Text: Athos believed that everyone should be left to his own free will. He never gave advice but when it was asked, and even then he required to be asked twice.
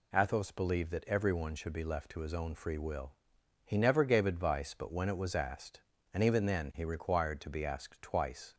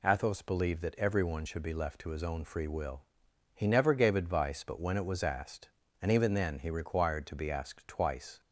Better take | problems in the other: neither | none

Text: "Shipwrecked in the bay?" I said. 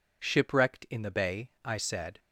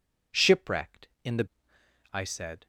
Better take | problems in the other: first | skips "bay"; at 1.7 s

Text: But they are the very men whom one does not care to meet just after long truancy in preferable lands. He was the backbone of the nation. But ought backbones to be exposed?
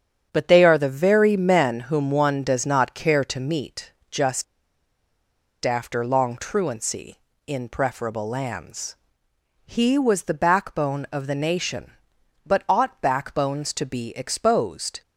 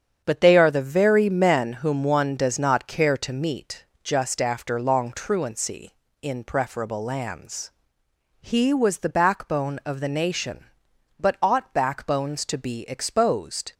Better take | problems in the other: second | starts louder than the rest; strong; until 1.3 s; 8 dB; strong in the second // pauses between "meet" and "just"; slight; at 3.9 s; 0.20 s long; slight in the second // pauses between "just" and "after"; at 4.4 s; 1.2 s long

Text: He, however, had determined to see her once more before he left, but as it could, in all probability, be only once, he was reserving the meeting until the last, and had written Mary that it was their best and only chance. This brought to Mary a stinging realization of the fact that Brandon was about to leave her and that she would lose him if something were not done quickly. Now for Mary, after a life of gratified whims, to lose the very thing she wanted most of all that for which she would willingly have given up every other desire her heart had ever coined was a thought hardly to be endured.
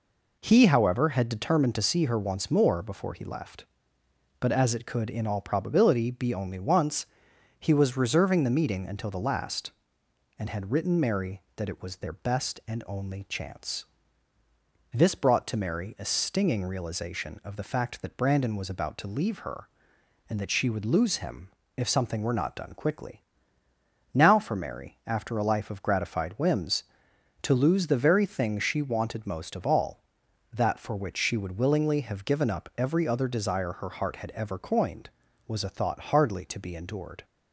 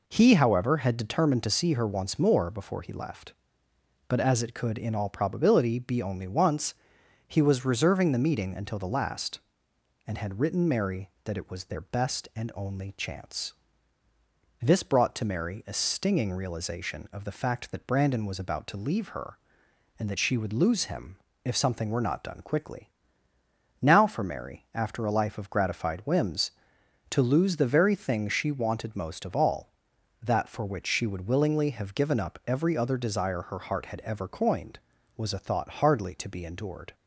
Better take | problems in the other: neither | pauses between "him" and "if"; slight; the same in both

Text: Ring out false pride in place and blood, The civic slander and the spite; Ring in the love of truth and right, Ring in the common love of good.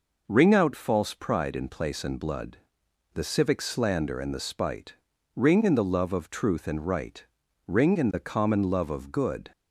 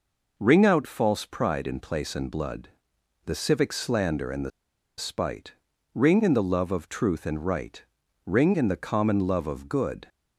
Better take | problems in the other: first | pauses between "the" and "spite"; noticeable; at 4.5 s; 0.47 s long

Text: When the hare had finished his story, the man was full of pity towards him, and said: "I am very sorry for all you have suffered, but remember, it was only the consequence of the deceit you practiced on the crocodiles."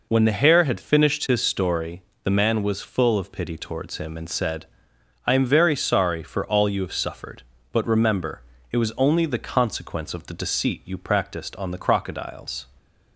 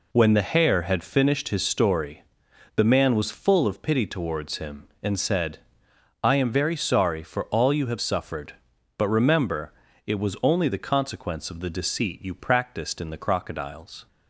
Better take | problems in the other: first | says "in" for "on"; at 12.9 s

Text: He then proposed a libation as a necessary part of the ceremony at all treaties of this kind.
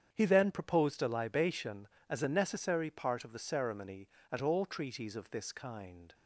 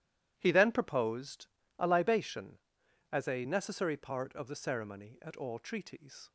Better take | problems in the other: first | starts louder than the rest; strong; until 1.3 s; 12.5 dB; strong in the first // pauses between "proposed" and "a"; slight; at 1.4 s; 0.32 s long // stops before "of this kind"; at 6.2 s

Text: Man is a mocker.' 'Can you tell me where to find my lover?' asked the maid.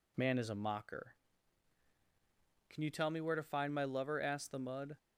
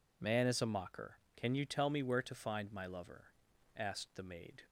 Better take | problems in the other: second | says "mud" for "maid"; at 4.5 s

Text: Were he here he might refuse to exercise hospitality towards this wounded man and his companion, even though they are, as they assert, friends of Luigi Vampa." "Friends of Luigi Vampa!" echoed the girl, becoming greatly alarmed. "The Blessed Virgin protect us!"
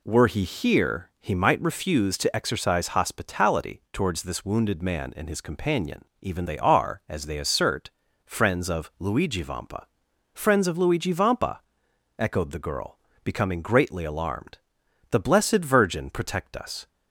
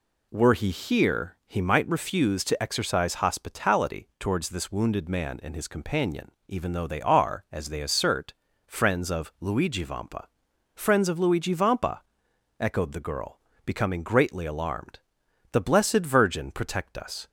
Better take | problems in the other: second | skips "though"; at 6.4 s

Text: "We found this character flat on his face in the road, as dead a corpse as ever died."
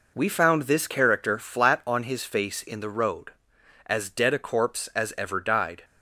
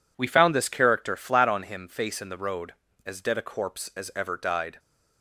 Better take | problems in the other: first | says "him" for "his"; at 1.6 s

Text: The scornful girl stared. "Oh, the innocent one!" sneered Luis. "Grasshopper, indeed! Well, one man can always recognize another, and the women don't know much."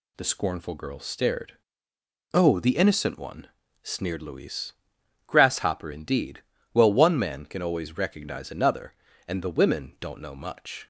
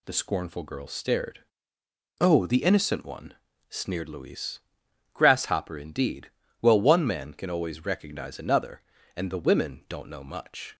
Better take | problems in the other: neither | none

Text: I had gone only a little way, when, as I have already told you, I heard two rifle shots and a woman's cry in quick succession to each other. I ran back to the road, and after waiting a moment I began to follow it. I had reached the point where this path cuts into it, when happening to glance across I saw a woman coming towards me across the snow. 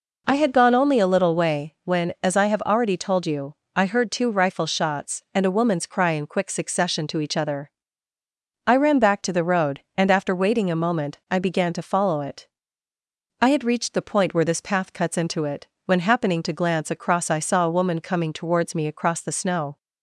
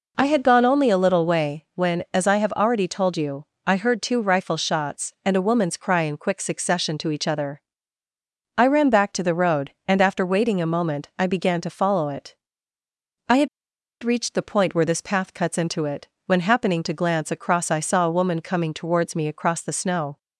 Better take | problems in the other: first | pauses between "had" and "reached"; noticeable; at 13.4 s; 0.55 s long

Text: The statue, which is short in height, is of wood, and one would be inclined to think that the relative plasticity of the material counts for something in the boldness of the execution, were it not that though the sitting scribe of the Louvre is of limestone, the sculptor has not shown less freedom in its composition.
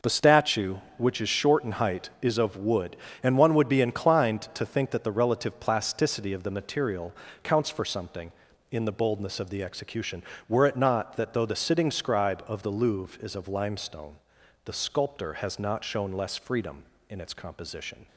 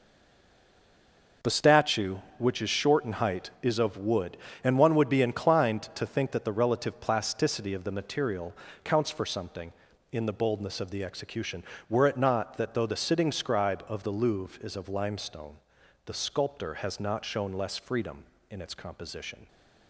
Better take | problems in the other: first | stays silent before the first word; noticeable; until 1.4 s; 1.4 s long // pauses between "material" and "counts"; slight; at 8.5 s; 0.30 s long; slight in the first

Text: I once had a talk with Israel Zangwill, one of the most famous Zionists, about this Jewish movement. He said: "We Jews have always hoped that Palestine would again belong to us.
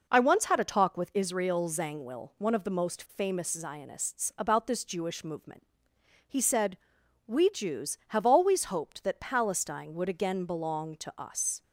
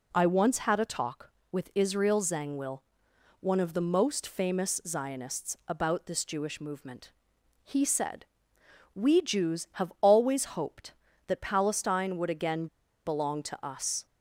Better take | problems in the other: first | pauses between "again" and "belong"; at 12.6 s; 0.40 s long

